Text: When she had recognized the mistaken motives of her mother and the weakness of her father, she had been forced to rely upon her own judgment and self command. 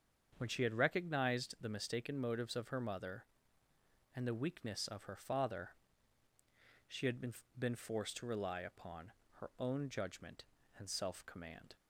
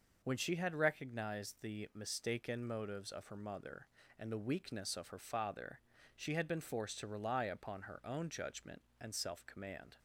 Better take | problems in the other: second | starts louder than the rest; until 1.3 s; 7 dB // says "been" twice; at 7.5 s // pauses between "upon" and "her"; slight; at 9.1 s; 0.28 s long

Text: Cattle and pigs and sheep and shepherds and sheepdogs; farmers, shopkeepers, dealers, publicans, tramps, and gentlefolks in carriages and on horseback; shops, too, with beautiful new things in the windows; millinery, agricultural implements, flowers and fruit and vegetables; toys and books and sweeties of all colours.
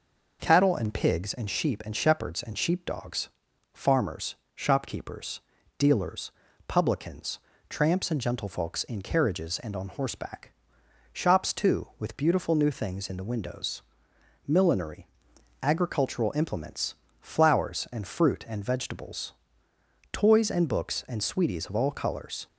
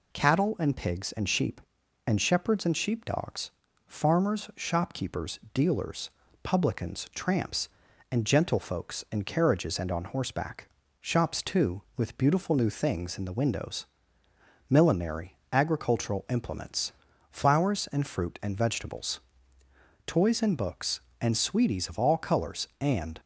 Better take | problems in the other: first | goes on to say "And"; slight; from 22.7 s on; 0.40 s long

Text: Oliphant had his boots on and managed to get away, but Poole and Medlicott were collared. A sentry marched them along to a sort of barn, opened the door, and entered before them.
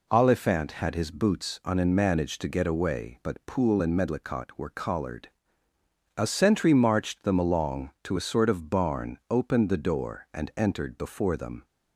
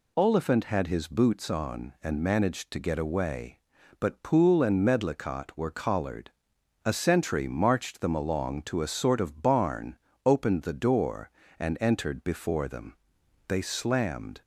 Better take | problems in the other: first | goes on to say "They slammed"; noticeable; from 13.4 s on; 0.94 s long

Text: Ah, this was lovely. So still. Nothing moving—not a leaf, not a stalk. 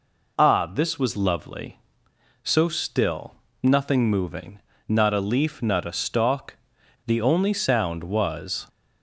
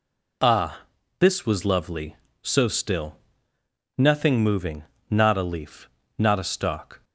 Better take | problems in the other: second | goes on to say "The only sound was"; from 7.0 s on; 1.6 s long

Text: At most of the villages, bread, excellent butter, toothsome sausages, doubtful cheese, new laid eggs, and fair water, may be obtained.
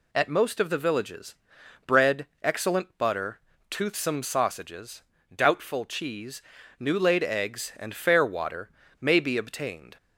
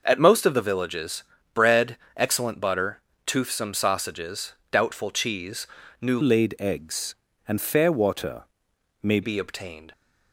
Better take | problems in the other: first | changes voice from "laid" to "may"; from 6.2 to 9.2 s; 3.0 s long

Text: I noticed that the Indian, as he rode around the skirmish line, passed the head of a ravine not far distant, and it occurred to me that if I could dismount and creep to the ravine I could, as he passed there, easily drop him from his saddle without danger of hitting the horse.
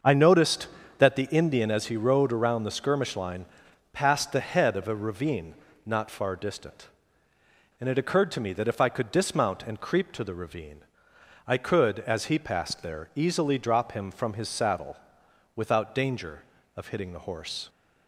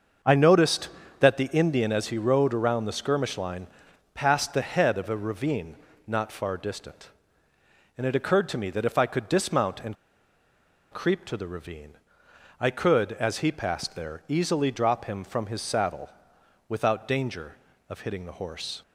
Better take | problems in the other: first | starts louder than the rest; until 1.5 s; 6.5 dB; also in the first // pauses between "ravine" and "not"; slight; at 5.7 s; 0.30 s long; slight in the first // pauses between "and" and "creep"; noticeable; at 9.9 s; 0.98 s long // pauses between "ravine" and "I"; noticeable; at 11.9 s; 0.66 s long; noticeable in the first // pauses between "saddle" and "without"; noticeable; at 16.0 s; 0.58 s long; noticeable in the first

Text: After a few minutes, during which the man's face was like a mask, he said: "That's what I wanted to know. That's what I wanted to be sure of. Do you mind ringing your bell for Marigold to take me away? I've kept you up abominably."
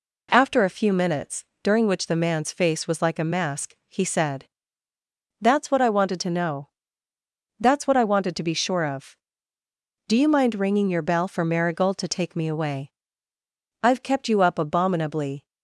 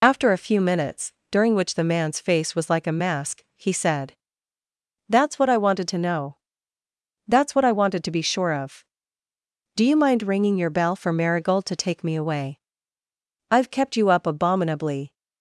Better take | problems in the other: first | loses the start of "After"; at 0.0 s; 60 ms

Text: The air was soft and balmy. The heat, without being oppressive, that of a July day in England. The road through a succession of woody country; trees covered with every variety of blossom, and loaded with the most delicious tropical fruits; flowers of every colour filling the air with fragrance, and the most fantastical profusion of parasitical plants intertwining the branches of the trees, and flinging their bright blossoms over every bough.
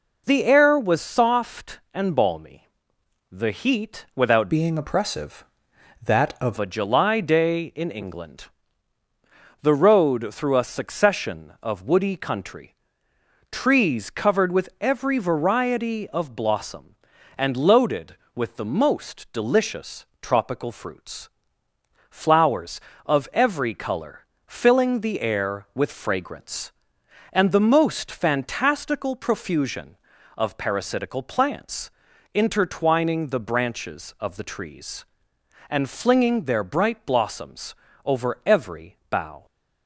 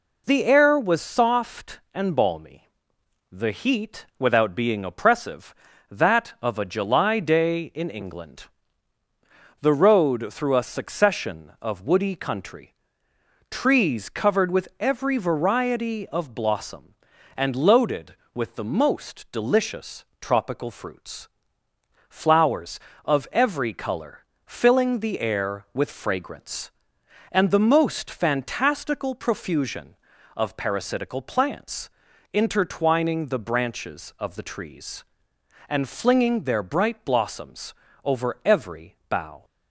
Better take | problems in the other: second | changes voice from "being" to "of"; from 4.4 to 6.5 s; 2.1 s long // pauses between "delicious" and "tropical"; slight; at 20.0 s; 0.16 s long; slight in the second // pauses between "colour" and "filling"; slight; at 24.2 s; 0.20 s long; slight in the second // pauses between "plants" and "intertwining"; at 31.9 s; 0.42 s long; also in the second // pauses between "blossoms" and "over"; slight; at 37.7 s; 0.30 s long; slight in the second

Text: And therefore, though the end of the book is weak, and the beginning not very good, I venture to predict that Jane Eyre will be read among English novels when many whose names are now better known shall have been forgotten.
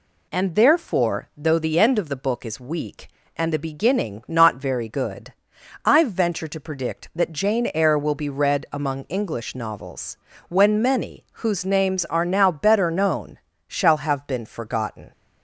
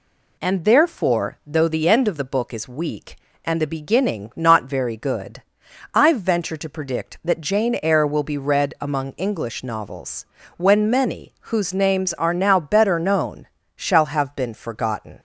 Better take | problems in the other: neither | pauses between "novels" and "when"; slight; the same in both // pauses between "known" and "shall"; slight; the same in both

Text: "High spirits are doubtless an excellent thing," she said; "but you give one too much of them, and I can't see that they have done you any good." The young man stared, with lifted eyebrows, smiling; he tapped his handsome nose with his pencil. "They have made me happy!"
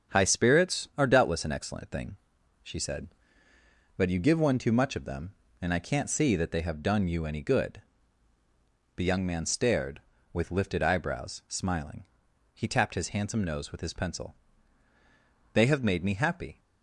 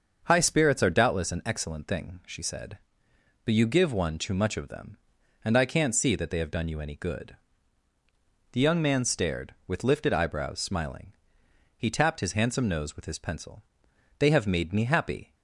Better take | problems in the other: neither | starts louder than the rest; the same in both

